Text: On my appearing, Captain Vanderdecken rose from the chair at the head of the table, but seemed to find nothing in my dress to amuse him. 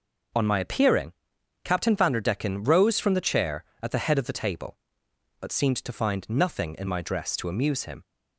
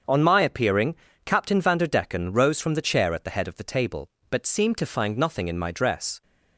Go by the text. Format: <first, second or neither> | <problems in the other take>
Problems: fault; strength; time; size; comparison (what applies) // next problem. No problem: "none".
first | starts louder than the rest; until 1.3 s; 6.5 dB // stops before "to amuse him"; at 6.2 s